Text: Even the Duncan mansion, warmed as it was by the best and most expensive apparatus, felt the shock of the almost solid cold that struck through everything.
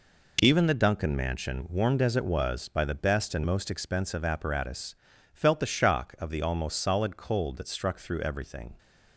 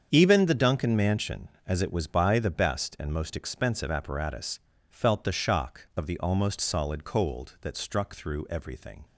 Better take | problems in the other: first | starts louder than the rest; strong; until 1.1 s; 7.5 dB // skips "warmed"; at 1.5 s

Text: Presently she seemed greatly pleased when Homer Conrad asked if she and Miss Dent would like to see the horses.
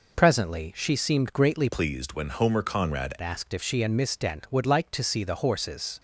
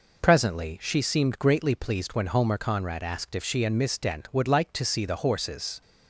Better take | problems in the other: second | changes voice from "pleased" to "Conrad"; from 1.6 to 3.1 s; 1.5 s long

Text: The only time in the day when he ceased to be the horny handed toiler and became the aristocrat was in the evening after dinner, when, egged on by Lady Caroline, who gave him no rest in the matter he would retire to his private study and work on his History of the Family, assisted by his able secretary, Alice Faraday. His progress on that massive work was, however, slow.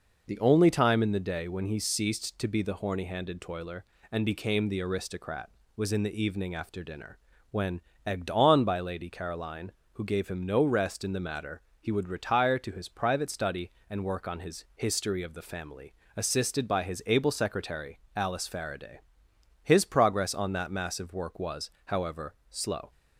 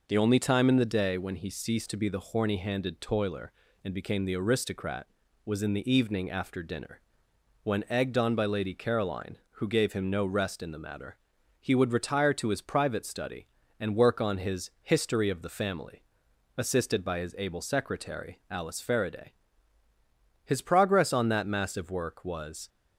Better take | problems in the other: first | pauses between "matter" and "he"; at 11.1 s; 0.44 s long; slight in the first // stops before "however slow"; at 22.6 s

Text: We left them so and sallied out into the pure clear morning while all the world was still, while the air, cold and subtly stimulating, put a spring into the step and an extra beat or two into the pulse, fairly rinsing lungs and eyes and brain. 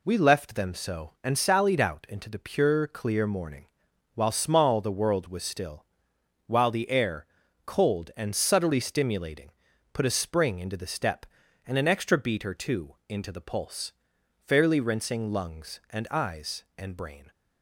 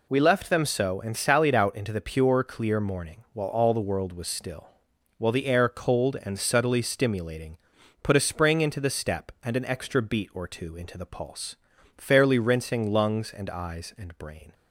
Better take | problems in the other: second | pauses between "morning" and "while"; noticeable; at 3.6 s; 0.48 s long // says "small" for "all"; at 4.3 s

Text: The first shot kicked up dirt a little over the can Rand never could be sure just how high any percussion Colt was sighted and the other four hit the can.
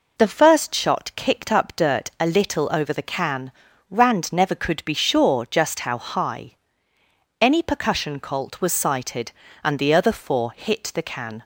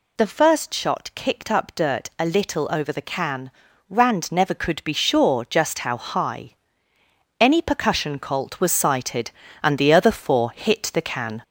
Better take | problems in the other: first | gets louder; slight; throughout; 2.5 dB // pauses between "can" and "Rand"; at 3.5 s; 0.40 s long; also in the first // pauses between "high" and "any"; noticeable; at 6.5 s; 0.84 s long; noticeable in the first

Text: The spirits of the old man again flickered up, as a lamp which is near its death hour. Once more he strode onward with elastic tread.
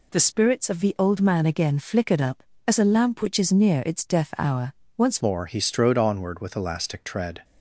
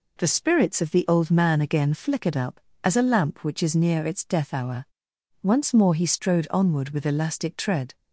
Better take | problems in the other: second | changes voice at "more"; from 5.2 s on; 2.2 s long

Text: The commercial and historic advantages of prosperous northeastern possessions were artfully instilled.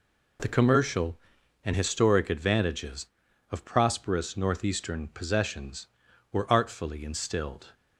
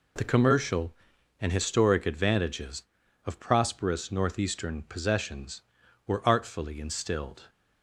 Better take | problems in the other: neither | none

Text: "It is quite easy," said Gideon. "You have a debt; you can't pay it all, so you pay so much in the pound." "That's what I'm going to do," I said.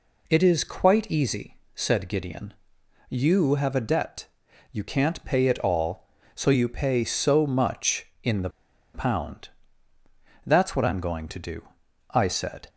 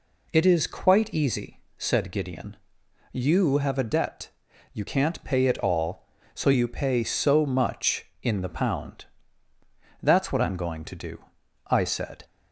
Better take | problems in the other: second | pauses between "the" and "pound"; at 8.4 s; 0.44 s long

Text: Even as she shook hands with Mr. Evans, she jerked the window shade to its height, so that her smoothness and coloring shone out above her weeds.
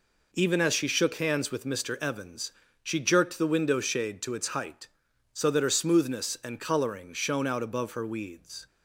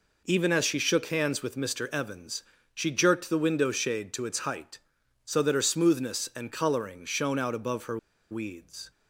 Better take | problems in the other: first | pauses between "her" and "weeds"; slight; at 7.9 s; 0.33 s long

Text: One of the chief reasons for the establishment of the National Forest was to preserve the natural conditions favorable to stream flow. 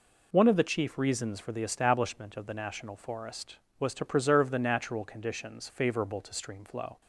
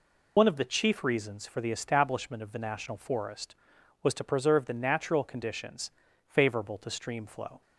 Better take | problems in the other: first | loses the start of "One"; at 0.3 s; 55 ms // pauses between "conditions" and "favorable"; at 5.8 s; 0.38 s long

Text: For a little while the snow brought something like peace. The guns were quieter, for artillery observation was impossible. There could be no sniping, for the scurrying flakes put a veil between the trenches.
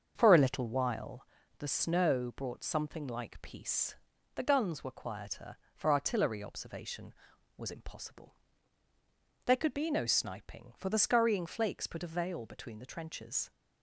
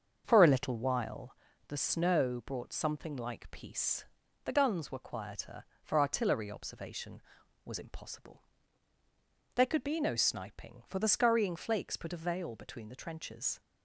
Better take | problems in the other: neither | starts louder than the rest; the same in both // pauses between "while" and "the"; slight; the same in both

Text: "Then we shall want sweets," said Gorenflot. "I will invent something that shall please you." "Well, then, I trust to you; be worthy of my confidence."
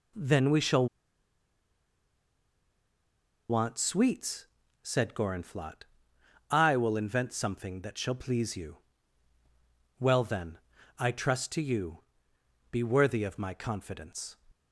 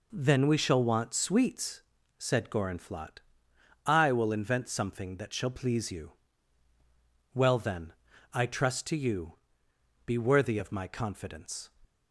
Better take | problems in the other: second | pauses between "shall" and "want"; strong; at 0.8 s; 2.6 s long

